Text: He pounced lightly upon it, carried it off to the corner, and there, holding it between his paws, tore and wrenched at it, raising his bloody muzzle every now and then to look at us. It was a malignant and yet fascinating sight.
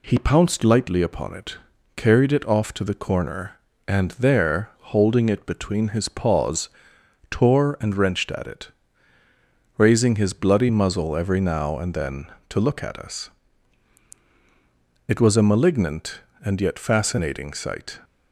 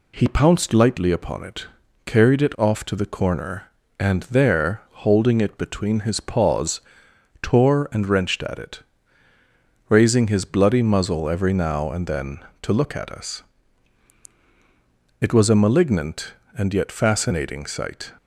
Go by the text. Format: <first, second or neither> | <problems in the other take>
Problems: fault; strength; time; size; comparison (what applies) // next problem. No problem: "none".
neither | none